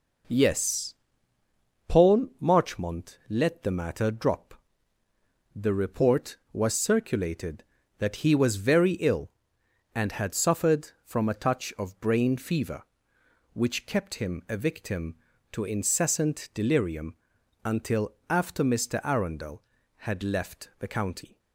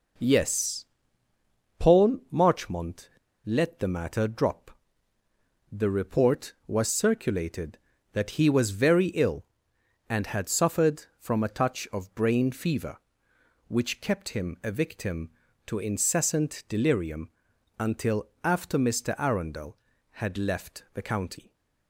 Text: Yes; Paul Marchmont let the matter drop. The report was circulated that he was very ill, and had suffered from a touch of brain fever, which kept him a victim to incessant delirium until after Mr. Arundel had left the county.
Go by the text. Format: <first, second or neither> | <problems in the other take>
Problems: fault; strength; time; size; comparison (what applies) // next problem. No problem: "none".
first | pauses between "Marchmont" and "let"; slight; at 3.0 s; 0.35 s long // pauses between "delirium" and "until"; noticeable; at 17.2 s; 0.50 s long; noticeable in the first // pauses between "until" and "after"; slight; at 18.2 s; 0.16 s long; slight in the first